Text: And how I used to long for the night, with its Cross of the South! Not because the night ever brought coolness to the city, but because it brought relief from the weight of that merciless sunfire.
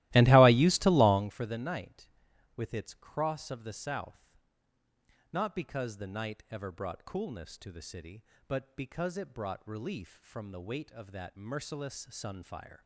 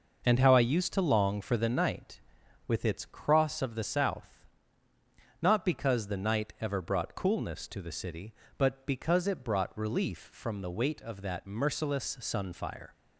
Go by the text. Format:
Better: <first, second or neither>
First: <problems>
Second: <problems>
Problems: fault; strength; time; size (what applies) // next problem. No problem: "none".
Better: second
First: starts louder than the rest; strong; until 1.4 s; 17 dB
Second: none